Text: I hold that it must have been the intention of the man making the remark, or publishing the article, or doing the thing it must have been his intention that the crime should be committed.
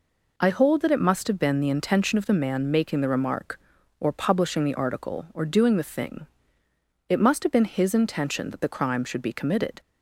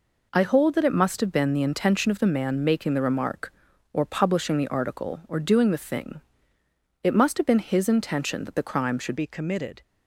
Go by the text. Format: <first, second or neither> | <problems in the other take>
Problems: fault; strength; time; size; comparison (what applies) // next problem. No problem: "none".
first | pauses between "thing" and "it"; noticeable; at 6.2 s; 0.80 s long; noticeable in the first // changes voice at "be"; from 9.1 s on; 0.7 s long